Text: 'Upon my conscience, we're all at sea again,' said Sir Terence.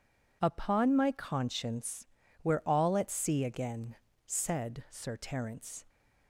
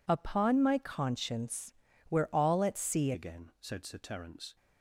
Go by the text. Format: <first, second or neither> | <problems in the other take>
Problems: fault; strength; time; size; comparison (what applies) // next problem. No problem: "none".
first | changes voice at "again"; from 3.1 s on; 1.4 s long